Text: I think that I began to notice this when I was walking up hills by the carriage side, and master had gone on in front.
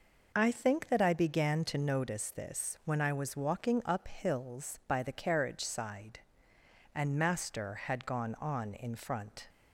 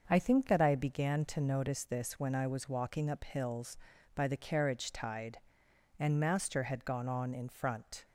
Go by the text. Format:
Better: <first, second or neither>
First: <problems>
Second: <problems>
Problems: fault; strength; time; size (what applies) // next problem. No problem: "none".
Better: first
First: none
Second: starts louder than the rest; until 1.0 s; 6.5 dB // says "tide" for "side"; at 4.9 s